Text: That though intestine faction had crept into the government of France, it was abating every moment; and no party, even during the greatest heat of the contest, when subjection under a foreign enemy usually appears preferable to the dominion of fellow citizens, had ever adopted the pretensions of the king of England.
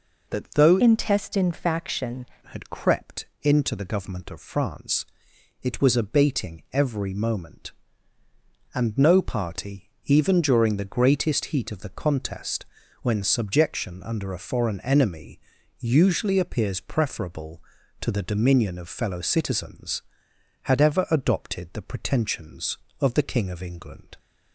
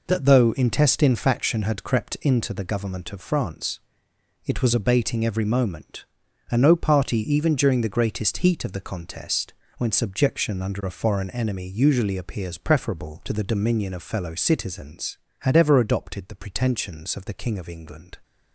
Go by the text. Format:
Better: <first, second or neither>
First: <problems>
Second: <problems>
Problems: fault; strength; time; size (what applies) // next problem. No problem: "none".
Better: second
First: changes voice from "intestine" to "faction"; from 0.8 to 2.2 s; 1.4 s long // pauses between "crept" and "into"; slight; at 3.2 s; 0.16 s long // pauses between "enemy" and "usually"; at 15.3 s; 0.42 s long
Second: none